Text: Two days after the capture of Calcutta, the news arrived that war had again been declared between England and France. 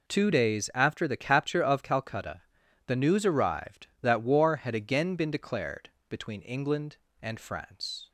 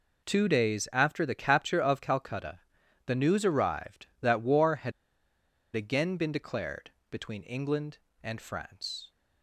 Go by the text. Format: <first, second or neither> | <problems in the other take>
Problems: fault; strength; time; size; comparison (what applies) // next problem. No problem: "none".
first | pauses between "had" and "again"; noticeable; at 4.9 s; 0.83 s long // pauses between "declared" and "between"; slight; at 6.8 s; 0.22 s long; slight in the first